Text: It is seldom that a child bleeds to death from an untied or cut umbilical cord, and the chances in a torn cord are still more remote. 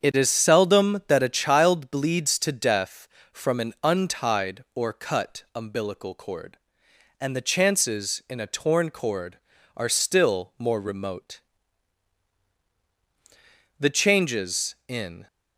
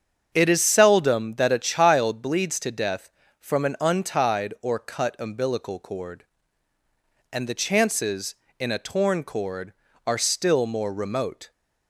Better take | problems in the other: second | starts louder than the rest; strong; until 1.1 s; 7.5 dB; strong in the second // goes on to say "The changes in"; from 13.7 s on; 1.4 s long

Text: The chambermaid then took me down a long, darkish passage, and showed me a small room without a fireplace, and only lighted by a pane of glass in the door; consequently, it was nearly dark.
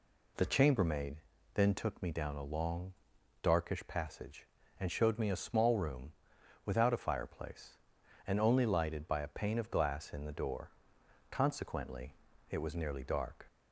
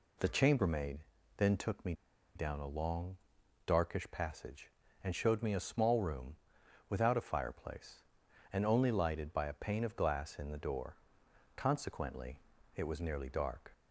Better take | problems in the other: first | pauses between "chambermaid" and "then"; at 0.9 s; 0.38 s long; also in the first // pauses between "me" and "down"; at 1.9 s; 0.42 s long // pauses between "room" and "without"; noticeable; at 6.3 s; 0.54 s long; noticeable in the first

